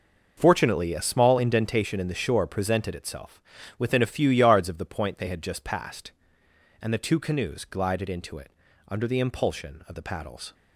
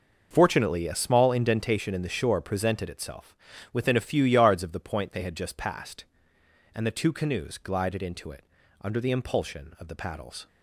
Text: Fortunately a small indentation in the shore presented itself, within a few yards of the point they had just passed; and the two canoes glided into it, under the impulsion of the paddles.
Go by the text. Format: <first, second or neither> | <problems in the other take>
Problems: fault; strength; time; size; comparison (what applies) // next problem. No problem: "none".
neither | none